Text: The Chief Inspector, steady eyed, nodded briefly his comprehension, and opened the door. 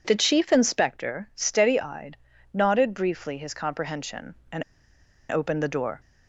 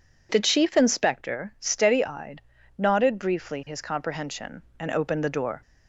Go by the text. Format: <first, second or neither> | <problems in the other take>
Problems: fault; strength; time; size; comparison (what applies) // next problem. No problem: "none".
second | pauses between "and" and "opened"; noticeable; at 4.6 s; 0.67 s long